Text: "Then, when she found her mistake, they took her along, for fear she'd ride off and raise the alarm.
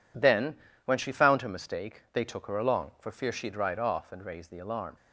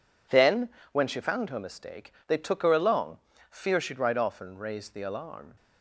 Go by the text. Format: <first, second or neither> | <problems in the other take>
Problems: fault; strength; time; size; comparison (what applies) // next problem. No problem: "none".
first | skips "for"; at 3.3 s